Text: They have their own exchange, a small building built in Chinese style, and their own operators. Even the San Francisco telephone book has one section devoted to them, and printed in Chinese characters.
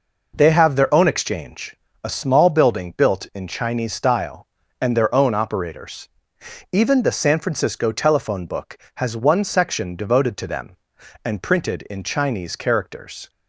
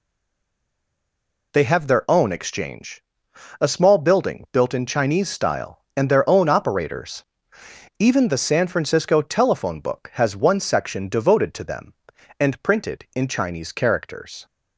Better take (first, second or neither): first